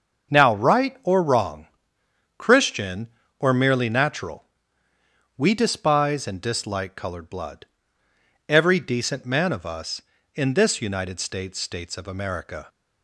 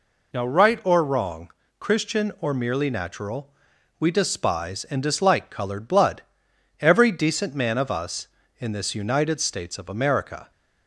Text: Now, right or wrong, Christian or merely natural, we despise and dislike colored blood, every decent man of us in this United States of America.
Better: second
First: starts louder than the rest; until 1.3 s; 7 dB // says "States" twice; at 11.5 s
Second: none

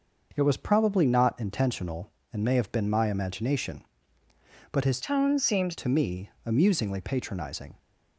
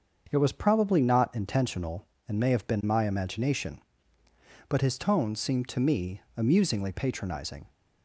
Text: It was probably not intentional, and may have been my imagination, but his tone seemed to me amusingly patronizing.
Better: second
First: starts louder than the rest; noticeable; until 1.3 s; 6 dB // changes voice from "tone" to "seemed"; from 5.0 to 5.7 s; 0.7 s long // pauses between "me" and "amusingly"; slight; at 6.2 s; 0.16 s long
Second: starts louder than the rest; until 1.3 s; 7 dB // pauses between "me" and "amusingly"; slight; at 6.2 s; 0.16 s long

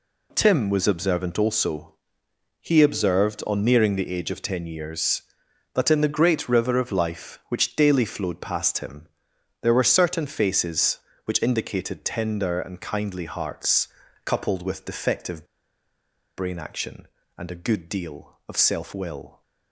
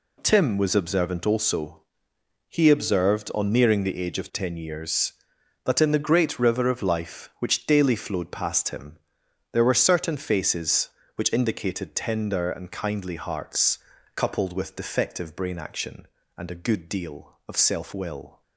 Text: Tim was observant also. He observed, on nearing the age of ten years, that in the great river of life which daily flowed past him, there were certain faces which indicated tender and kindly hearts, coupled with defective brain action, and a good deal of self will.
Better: second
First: pauses between "defective" and "brain"; noticeable; at 15.4 s; 0.92 s long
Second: none

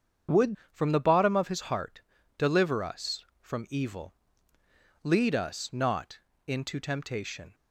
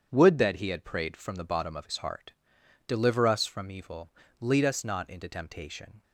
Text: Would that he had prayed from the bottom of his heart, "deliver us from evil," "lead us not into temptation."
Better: second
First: starts louder than the rest; strong; until 1.4 s; 7.5 dB // skips "that he had prayed"; at 0.6 s // pauses between "not" and "into"; slight; at 6.1 s; 0.28 s long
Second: starts louder than the rest; strong; until 1.1 s; 8 dB

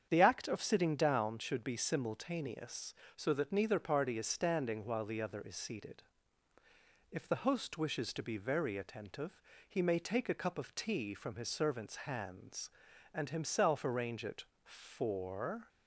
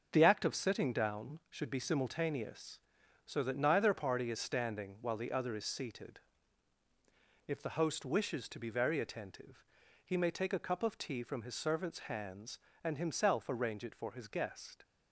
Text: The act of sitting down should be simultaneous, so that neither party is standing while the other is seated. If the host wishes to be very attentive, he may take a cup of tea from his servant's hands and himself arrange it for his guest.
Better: second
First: starts louder than the rest; strong; until 1.1 s; 8 dB // stops before "his guest"; at 15.6 s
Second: starts louder than the rest; until 1.1 s; 6.5 dB

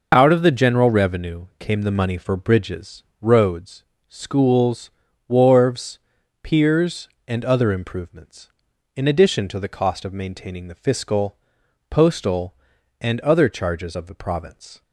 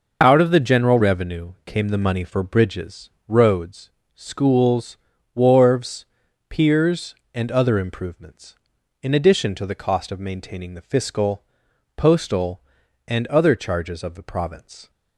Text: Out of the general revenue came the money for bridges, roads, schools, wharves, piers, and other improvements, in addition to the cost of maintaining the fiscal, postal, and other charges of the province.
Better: neither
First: none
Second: none

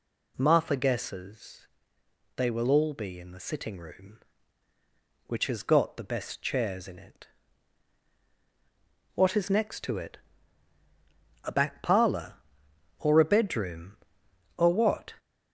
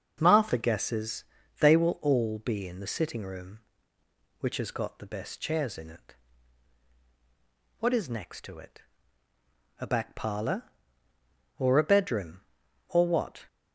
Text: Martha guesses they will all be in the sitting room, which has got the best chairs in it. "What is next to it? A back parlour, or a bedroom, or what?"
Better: second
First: gets louder; throughout; 3.5 dB // pauses between "guesses" and "they"; noticeable; at 1.6 s; 0.74 s long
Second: pauses between "guesses" and "they"; at 1.2 s; 0.38 s long

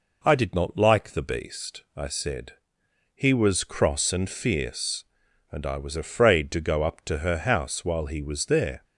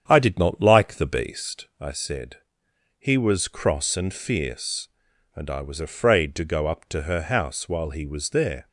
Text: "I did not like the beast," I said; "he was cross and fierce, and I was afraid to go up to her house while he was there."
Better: first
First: none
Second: starts louder than the rest; strong; until 1.8 s; 8.5 dB

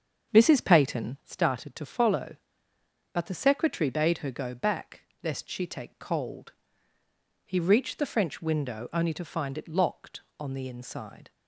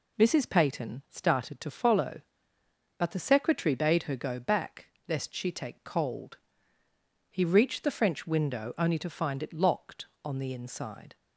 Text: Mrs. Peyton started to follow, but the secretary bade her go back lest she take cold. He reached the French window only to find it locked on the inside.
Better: second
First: starts louder than the rest; until 1.3 s; 7 dB // pauses between "back" and "lest"; slight; at 5.0 s; 0.22 s long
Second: pauses between "back" and "lest"; slight; at 4.8 s; 0.22 s long

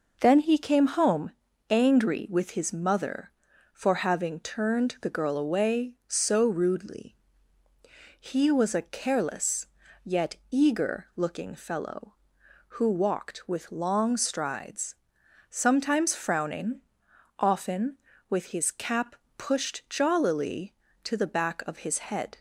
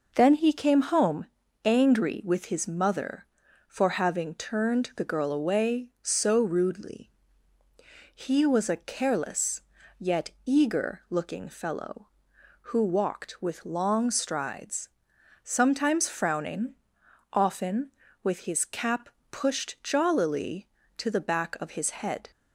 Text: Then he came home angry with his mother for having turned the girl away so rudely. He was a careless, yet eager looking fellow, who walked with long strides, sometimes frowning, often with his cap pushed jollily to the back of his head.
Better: neither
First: pauses between "home" and "angry"; at 1.3 s; 0.38 s long // pauses between "cap" and "pushed"; slight; at 19.1 s; 0.22 s long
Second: pauses between "home" and "angry"; at 1.2 s; 0.38 s long // pauses between "cap" and "pushed"; slight; at 19.0 s; 0.22 s long

